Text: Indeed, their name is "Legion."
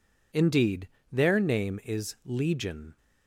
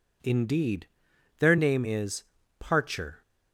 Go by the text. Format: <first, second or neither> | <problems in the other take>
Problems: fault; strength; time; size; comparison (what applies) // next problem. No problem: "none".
first | says "Parcher" for "Legion"; at 2.5 s